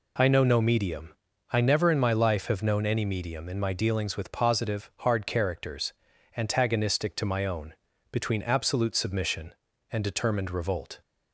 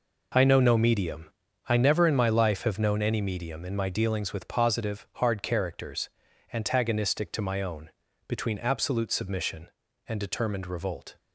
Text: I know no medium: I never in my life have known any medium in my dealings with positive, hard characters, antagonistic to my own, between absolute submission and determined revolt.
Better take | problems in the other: first | gets quieter; strong; throughout; 10.5 dB

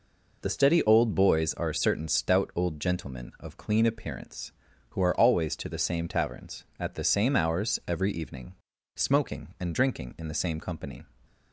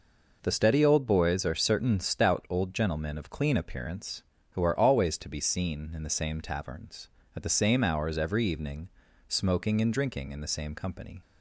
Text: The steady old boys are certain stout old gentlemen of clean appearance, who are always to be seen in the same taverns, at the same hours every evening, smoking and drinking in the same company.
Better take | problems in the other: second | skips "be seen in"; at 5.6 s

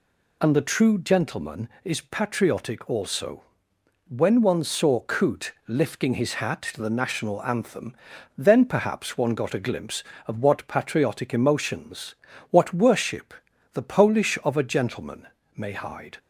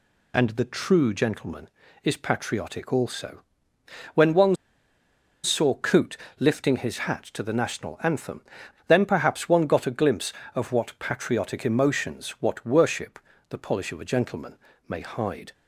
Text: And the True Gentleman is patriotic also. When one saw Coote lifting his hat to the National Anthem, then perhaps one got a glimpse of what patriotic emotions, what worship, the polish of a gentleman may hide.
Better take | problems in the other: first | pauses between "one" and "saw"; noticeable; at 4.5 s; 0.88 s long // pauses between "Coote" and "lifting"; slight; at 6.1 s; 0.20 s long // pauses between "gentleman" and "may"; slight; at 14.5 s; 0.32 s long; slight in the first

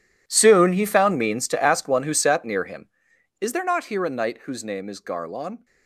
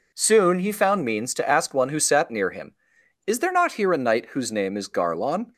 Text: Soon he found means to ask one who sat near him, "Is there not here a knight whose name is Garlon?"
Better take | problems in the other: second | gets quieter; strong; throughout; 17 dB

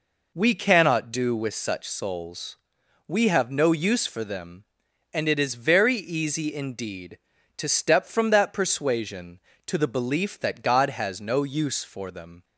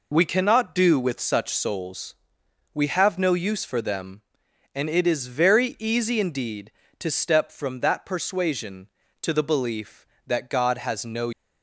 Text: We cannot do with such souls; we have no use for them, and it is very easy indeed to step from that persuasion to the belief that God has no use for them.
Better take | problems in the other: first | stops before "use for them"; at 11.3 s

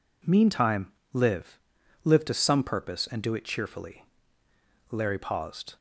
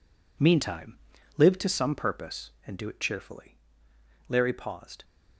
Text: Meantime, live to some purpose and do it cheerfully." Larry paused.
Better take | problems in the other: second | says "live" twice; at 2.0 s

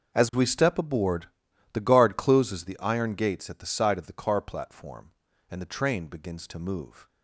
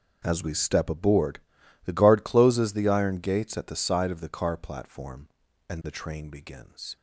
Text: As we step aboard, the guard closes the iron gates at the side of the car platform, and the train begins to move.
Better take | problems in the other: first | starts louder than the rest; until 1.2 s; 6 dB; noticeable in the first // stops before "to move"; at 6.9 s

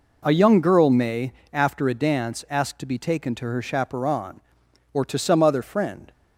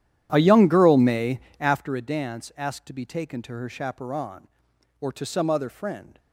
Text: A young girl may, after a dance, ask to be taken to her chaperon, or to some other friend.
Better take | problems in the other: first | starts louder than the rest; strong; until 1.9 s; 11 dB

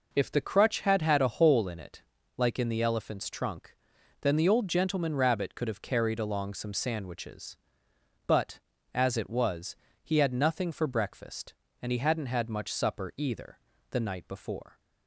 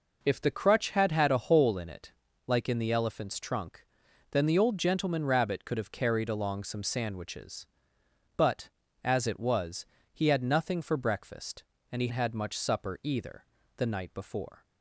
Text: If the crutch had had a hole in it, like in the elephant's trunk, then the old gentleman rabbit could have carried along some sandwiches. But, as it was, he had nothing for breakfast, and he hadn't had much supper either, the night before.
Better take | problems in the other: first | skips "hadn't"; at 12.0 s

